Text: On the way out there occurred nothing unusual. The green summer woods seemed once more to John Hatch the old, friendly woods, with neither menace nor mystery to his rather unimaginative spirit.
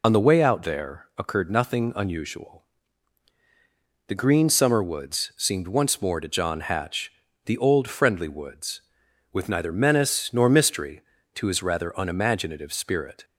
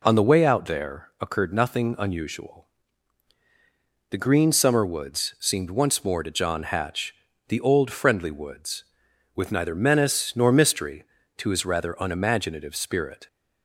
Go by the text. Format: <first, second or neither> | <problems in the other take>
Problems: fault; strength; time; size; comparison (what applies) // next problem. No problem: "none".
second | loses the start of "On"; at 0.0 s; 50 ms // pauses between "Hatch" and "the"; slight; at 7.1 s; 0.32 s long; slight in the second